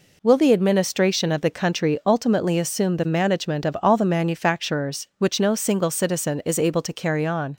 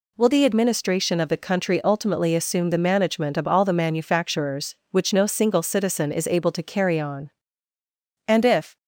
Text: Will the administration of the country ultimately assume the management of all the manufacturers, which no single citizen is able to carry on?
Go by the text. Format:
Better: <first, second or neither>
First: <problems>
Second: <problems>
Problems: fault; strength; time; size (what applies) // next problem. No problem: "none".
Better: first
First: none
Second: goes on to say "And if"; from 8.2 s on; 0.50 s long